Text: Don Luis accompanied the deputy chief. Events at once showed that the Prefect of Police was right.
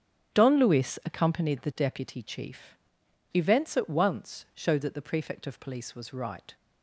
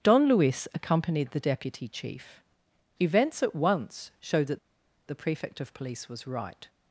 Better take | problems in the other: first | starts louder than the rest; strong; until 1.0 s; 8.5 dB; strong in the first // pauses between "that" and "the"; noticeable; at 4.5 s; 0.48 s long

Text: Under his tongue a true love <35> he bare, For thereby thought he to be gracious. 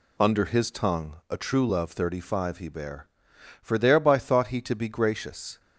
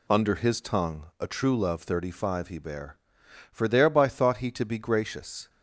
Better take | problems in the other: neither | none

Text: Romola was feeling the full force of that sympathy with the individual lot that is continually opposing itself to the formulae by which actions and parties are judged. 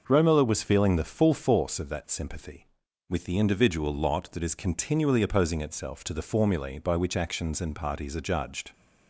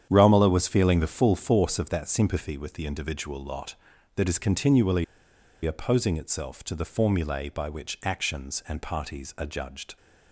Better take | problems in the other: first | starts louder than the rest; strong; until 1.1 s; 9 dB // pauses between "continually" and "opposing"; noticeable; at 5.0 s; 0.59 s long

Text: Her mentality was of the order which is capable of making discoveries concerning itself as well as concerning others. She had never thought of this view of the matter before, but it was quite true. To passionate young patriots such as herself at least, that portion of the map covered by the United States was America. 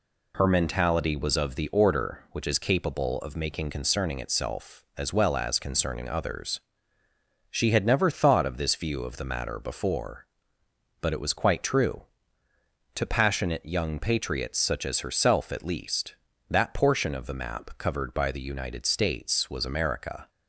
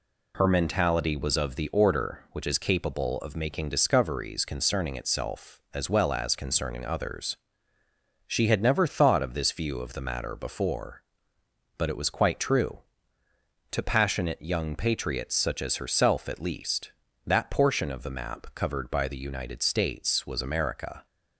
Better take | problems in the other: second | skips "discoveries"; at 3.6 s

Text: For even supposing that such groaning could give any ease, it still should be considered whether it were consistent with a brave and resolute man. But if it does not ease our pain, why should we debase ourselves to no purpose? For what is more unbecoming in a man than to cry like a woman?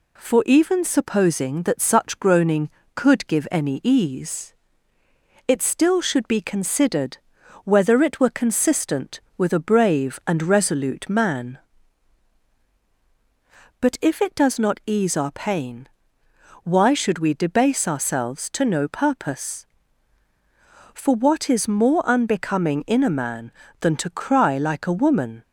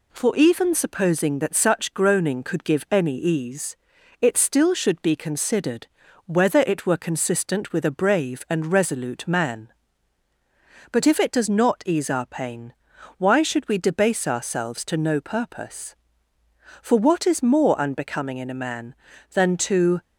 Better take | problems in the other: first | pauses between "considered" and "whether"; at 5.8 s; 0.40 s long; noticeable in the first // stops before "cry like a woman"; at 20.0 s

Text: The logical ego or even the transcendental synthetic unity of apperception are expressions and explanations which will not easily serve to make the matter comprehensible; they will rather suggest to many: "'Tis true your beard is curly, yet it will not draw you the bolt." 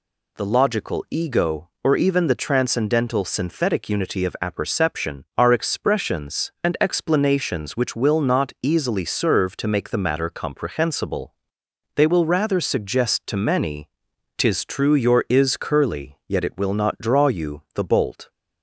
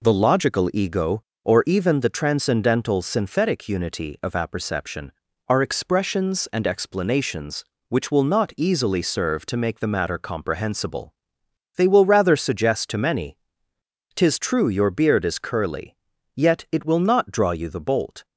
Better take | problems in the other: second | skips "beard"; at 15.2 s

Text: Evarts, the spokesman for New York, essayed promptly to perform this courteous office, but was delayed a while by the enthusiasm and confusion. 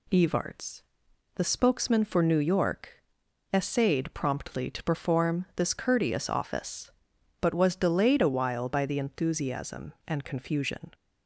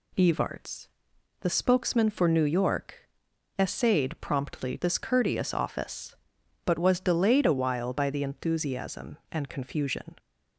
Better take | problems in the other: first | skips "to perform"; at 4.7 s

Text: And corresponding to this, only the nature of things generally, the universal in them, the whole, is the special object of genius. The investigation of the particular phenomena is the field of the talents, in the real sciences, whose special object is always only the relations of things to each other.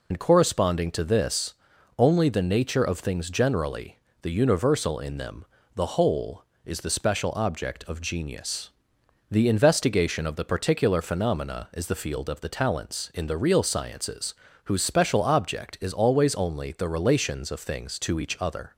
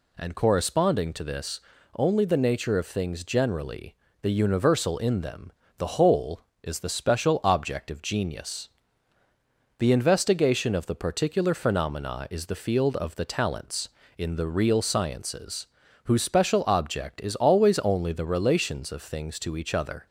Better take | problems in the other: second | loses the start of "And"; at 0.1 s; 90 ms

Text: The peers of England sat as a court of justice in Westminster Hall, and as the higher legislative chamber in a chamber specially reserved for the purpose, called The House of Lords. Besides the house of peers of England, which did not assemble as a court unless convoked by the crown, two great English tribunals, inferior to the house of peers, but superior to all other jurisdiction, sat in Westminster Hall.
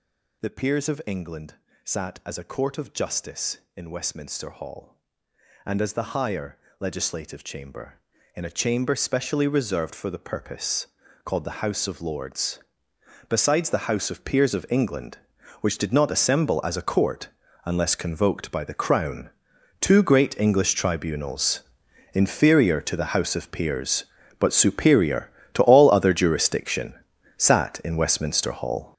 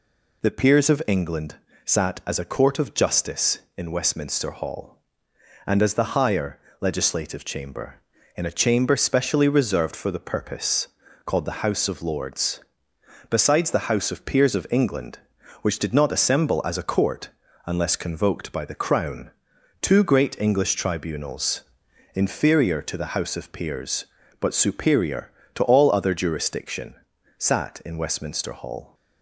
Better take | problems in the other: second | gets louder; strong; throughout; 11 dB // pauses between "England" and "sat"; slight; at 1.5 s; 0.28 s long; slight in the second // pauses between "higher" and "legislative"; slight; at 6.5 s; 0.20 s long; slight in the second // pauses between "court" and "unless"; slight; at 17.2 s; 0.36 s long; slight in the second

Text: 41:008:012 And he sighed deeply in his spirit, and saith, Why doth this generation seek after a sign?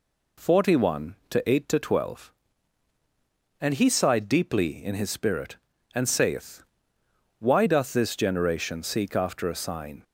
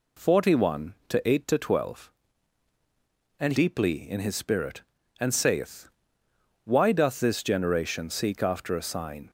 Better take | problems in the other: first | skips "he sighed"; at 3.5 s

